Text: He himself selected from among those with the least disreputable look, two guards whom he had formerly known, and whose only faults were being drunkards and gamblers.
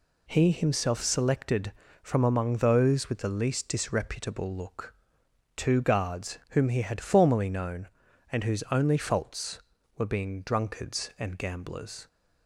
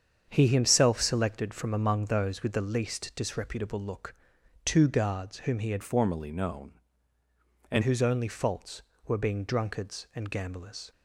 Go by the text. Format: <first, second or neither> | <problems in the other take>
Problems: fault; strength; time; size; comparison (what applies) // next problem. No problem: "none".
first | starts louder than the rest; strong; until 1.3 s; 7.5 dB // changes voice from "formerly" to "and"; from 5.8 to 7.8 s; 2.0 s long